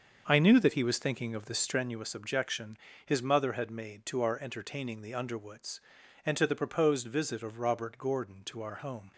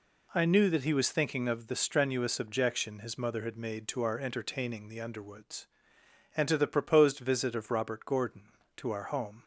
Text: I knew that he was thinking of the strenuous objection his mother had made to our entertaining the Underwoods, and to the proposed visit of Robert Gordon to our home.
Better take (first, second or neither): second